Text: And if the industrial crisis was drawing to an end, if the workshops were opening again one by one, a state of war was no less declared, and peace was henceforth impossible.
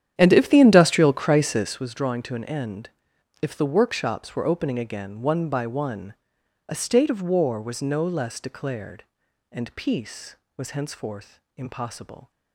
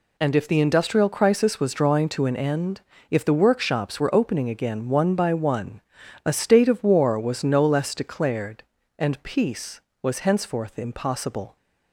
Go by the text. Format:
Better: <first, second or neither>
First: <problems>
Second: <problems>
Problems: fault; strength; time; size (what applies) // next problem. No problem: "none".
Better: second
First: starts louder than the rest; strong; until 1.9 s; 10 dB // pauses between "henceforth" and "impossible"; slight; at 11.4 s; 0.16 s long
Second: none